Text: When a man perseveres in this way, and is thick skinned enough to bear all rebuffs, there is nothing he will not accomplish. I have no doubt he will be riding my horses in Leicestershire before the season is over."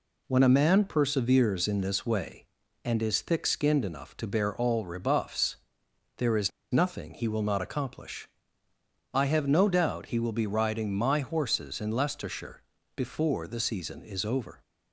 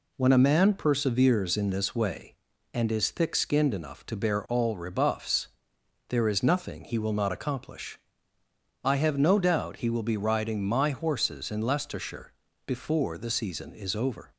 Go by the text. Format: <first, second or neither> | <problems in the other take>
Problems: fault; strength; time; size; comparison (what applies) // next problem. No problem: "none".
second | pauses between "is" and "nothing"; slight; at 6.4 s; 0.21 s long // pauses between "Leicestershire" and "before"; slight; at 12.6 s; 0.34 s long; slight in the second